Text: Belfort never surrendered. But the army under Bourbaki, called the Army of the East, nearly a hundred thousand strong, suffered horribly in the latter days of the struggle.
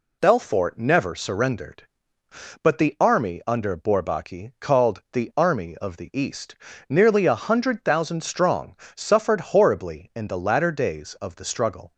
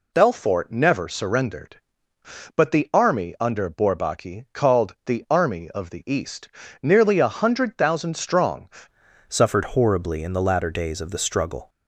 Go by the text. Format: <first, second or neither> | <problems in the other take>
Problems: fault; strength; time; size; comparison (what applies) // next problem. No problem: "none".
first | changes voice at "suffered"; from 9.2 s on; 2.4 s long